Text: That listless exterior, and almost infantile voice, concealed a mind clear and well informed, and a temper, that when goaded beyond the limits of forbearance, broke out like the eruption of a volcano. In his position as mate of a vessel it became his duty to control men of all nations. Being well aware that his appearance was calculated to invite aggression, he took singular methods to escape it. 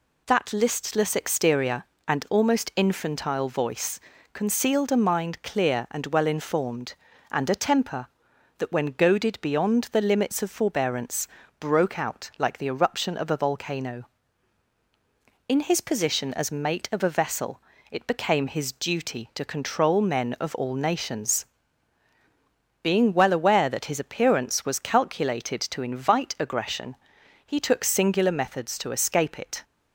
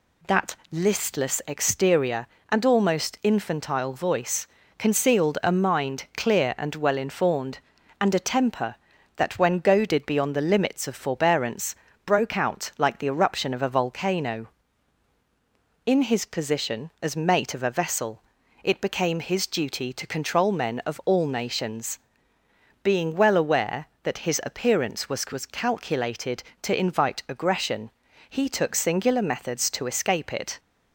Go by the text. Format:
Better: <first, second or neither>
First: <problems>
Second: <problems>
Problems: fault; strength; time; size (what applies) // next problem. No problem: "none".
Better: first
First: pauses between "vessel" and "it"; slight; at 17.5 s; 0.32 s long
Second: pauses between "That" and "listless"; slight; at 0.5 s; 0.16 s long // pauses between "vessel" and "it"; at 18.2 s; 0.42 s long // says "was" twice; at 25.3 s